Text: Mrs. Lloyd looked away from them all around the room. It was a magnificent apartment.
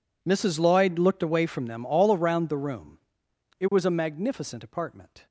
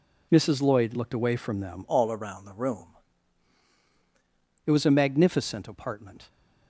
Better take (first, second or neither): first